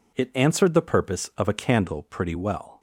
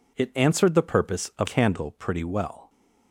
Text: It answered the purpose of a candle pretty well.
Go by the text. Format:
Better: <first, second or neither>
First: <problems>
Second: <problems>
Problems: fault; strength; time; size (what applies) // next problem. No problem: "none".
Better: first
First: none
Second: skips "a"; at 1.4 s